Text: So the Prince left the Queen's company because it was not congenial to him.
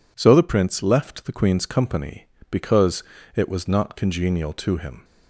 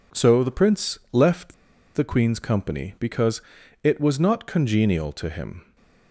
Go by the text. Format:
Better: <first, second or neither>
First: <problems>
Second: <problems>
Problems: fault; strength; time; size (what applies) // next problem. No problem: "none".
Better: first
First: pauses between "because" and "it"; slight; at 3.0 s; 0.32 s long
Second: pauses between "left" and "the"; at 1.5 s; 0.41 s long // pauses between "because" and "it"; at 3.4 s; 0.42 s long